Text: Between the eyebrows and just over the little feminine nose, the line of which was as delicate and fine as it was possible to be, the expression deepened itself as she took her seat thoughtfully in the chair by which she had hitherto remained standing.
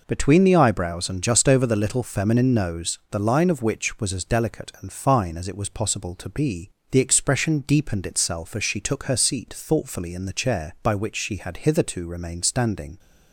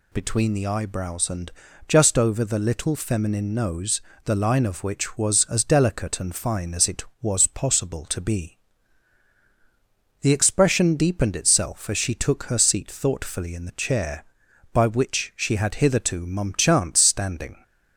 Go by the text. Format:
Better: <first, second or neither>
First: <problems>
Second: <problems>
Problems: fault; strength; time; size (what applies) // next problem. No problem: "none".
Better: first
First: none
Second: pauses between "and" and "just"; at 1.5 s; 0.38 s long // says "mumchance" for "remained"; at 16.2 s